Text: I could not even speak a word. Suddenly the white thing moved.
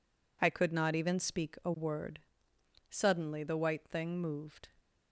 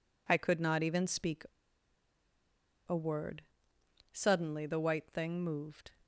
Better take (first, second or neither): first